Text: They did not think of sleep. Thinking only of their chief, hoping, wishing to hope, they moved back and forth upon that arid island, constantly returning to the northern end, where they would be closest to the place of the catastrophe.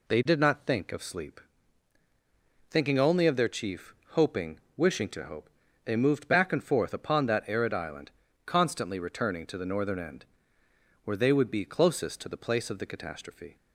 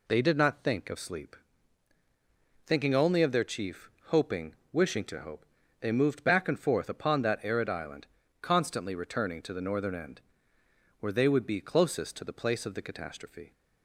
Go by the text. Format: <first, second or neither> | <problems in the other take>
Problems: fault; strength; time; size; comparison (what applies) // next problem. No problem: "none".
neither | none